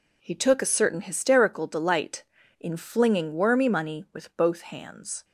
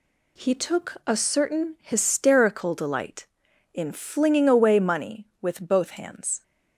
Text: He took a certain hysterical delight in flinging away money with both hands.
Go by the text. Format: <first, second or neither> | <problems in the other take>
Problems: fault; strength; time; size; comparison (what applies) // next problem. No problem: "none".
second | says "wormy" for "away"; at 3.3 s